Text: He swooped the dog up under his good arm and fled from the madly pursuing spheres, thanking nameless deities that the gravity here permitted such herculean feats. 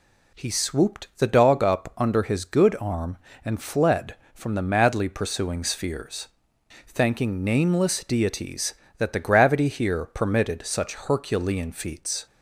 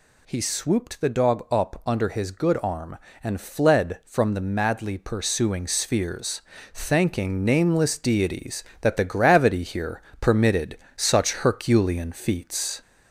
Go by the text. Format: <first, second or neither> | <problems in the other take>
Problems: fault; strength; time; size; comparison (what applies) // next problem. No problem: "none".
first | gets louder; slight; throughout; 2.5 dB // pauses between "here" and "permitted"; slight; at 10.0 s; 0.18 s long // pauses between "permitted" and "such"; slight; at 10.7 s; 0.18 s long